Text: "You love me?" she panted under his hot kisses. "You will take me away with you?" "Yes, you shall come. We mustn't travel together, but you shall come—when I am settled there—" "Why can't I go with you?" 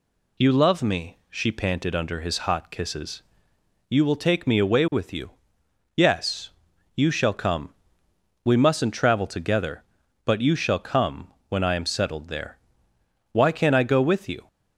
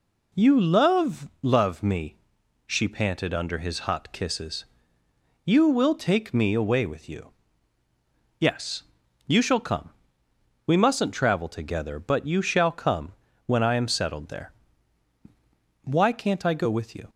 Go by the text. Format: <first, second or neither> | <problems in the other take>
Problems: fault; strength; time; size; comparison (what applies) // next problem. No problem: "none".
first | says "love" twice; at 1.4 s